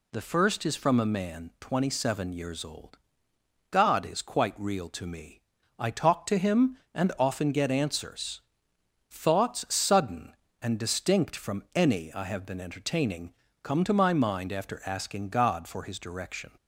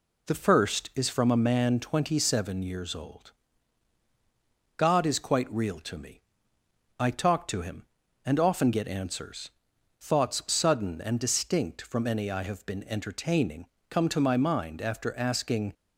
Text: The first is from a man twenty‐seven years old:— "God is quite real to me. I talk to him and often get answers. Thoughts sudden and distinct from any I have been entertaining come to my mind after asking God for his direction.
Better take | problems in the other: first | pauses between "entertaining" and "come"; slight; at 13.6 s; 0.24 s long; slight in the first // stops before "God for his direction"; at 15.7 s

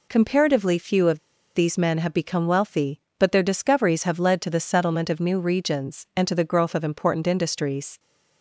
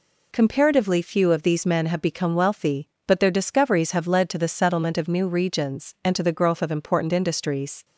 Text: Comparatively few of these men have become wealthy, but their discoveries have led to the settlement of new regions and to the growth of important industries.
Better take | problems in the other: second | pauses between "of" and "these"; at 1.1 s; 0.37 s long

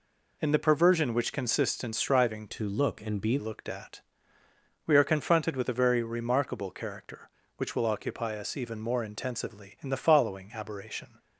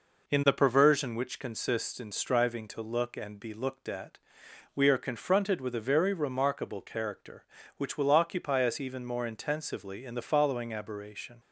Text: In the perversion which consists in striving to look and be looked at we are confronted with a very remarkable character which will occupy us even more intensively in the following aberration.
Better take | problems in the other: second | changes voice from "to" to "be"; from 2.4 to 3.3 s; 0.9 s long // pauses between "at" and "we"; noticeable; at 4.0 s; 0.86 s long; noticeable in the second

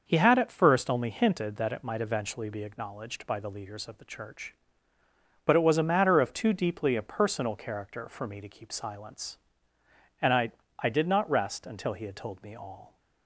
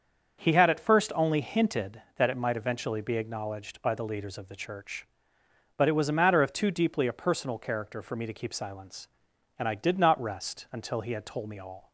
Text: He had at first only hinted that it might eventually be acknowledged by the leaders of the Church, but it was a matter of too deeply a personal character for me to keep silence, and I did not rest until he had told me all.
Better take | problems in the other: second | starts louder than the rest; until 1.0 s; 6 dB; also in the second // says "I" twice; at 10.7 s

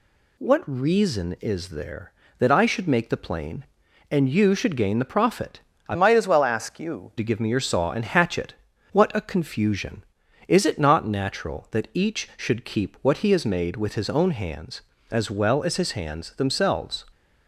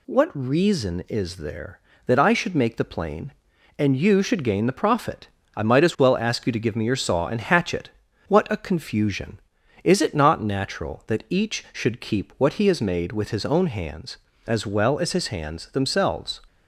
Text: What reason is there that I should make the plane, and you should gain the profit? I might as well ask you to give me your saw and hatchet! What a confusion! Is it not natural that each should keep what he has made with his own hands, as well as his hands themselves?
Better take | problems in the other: second | changes voice from "might" to "you"; from 5.9 to 7.1 s; 1.2 s long

